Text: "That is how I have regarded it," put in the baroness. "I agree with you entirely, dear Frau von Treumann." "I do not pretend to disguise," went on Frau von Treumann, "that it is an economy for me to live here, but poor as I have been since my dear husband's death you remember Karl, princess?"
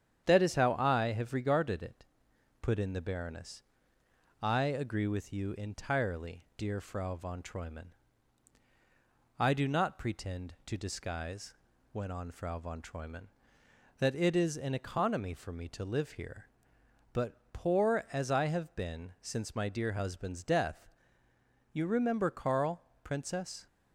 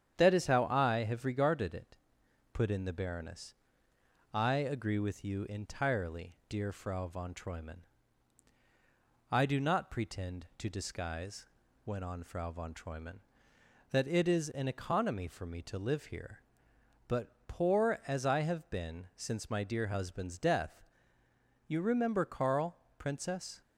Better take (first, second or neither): neither